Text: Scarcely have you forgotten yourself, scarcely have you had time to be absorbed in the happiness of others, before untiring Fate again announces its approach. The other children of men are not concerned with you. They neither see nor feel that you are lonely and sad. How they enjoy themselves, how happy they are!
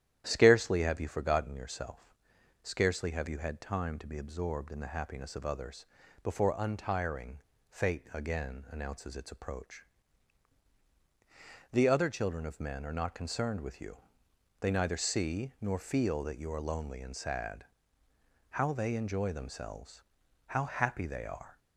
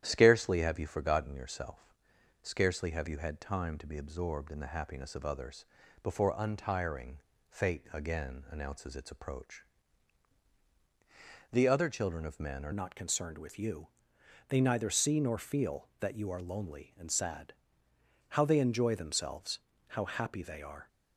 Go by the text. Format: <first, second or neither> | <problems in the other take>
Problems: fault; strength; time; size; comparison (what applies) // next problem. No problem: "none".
first | starts louder than the rest; strong; until 1.0 s; 10.5 dB; strong in the first // pauses between "untiring" and "Fate"; slight; at 7.1 s; 0.30 s long; slight in the first // changes voice at "not"; from 12.7 s on; 8.1 s long